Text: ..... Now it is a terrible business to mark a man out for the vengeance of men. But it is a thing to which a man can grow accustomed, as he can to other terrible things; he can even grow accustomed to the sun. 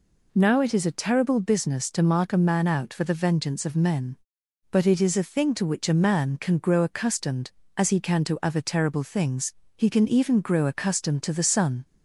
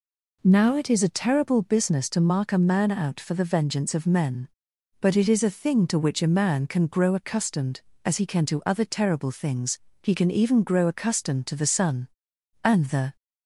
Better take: first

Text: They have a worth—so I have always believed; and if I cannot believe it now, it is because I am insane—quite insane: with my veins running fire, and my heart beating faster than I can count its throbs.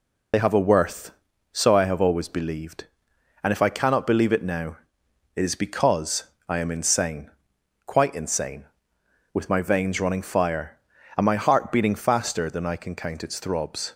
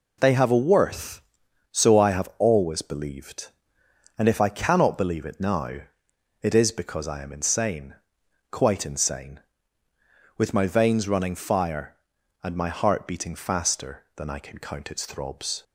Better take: second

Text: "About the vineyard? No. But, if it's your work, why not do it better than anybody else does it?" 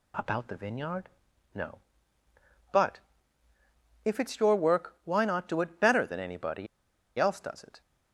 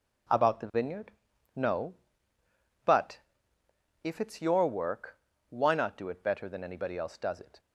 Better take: second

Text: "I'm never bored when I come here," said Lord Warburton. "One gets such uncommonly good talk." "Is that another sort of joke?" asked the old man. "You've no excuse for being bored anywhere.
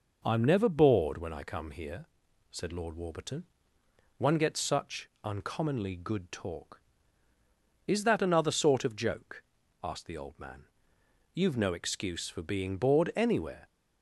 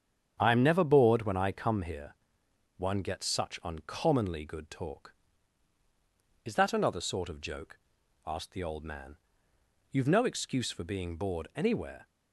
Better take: first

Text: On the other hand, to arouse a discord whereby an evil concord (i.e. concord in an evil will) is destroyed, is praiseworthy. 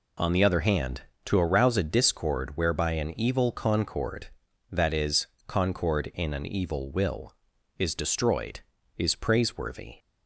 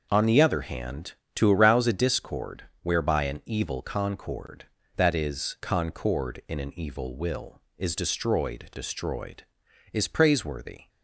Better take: first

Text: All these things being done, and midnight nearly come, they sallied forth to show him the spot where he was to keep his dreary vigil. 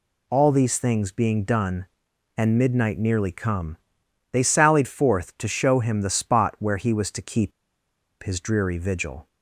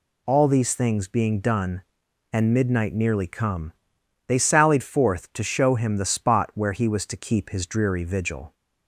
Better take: second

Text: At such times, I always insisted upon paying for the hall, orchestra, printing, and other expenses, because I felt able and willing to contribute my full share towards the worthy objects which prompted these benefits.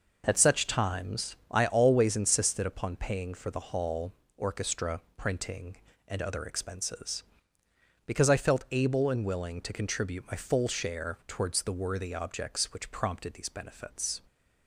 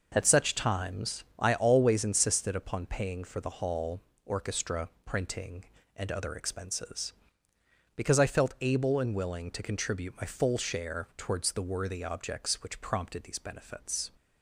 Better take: neither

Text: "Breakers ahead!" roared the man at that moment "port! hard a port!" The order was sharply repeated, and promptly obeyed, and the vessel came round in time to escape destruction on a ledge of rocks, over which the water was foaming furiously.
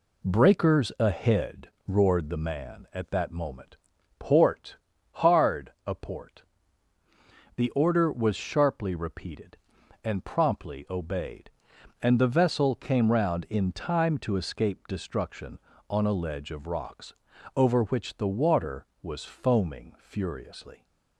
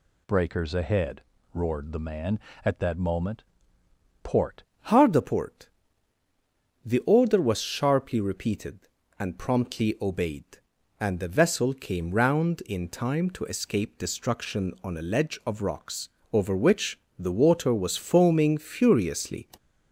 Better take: first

